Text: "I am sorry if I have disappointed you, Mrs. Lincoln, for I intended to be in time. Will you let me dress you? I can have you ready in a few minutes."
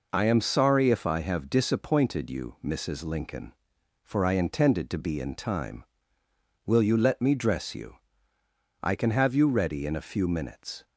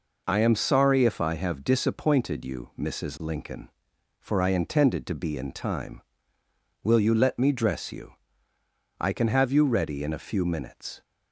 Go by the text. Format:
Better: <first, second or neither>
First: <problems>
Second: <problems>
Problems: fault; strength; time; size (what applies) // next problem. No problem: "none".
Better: neither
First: none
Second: none